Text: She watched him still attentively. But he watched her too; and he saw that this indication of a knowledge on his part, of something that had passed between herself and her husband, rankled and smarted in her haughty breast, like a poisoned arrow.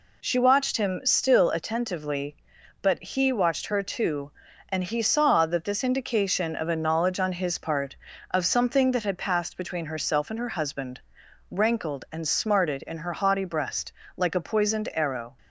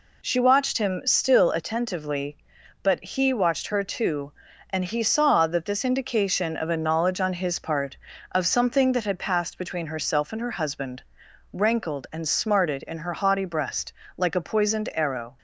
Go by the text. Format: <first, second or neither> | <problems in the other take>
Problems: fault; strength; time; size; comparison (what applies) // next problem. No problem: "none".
neither | none